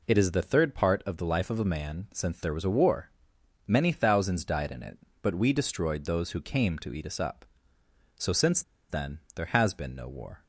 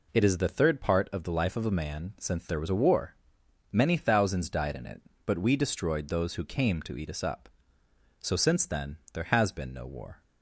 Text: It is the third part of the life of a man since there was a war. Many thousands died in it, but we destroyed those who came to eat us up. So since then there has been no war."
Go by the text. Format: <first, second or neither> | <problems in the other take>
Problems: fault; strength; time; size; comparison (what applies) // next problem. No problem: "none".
second | pauses between "since" and "then"; slight; at 8.6 s; 0.28 s long